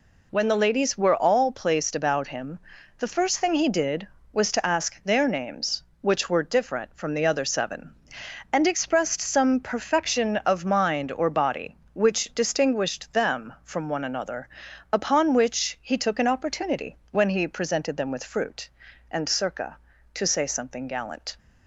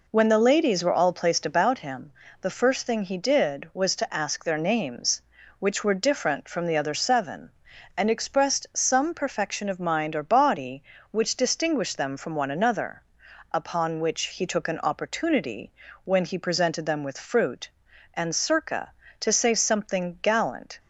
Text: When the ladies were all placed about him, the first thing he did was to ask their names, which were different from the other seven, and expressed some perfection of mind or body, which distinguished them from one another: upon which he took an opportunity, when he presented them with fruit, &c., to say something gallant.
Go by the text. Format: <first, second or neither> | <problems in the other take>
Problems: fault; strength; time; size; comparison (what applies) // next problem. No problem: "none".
neither | none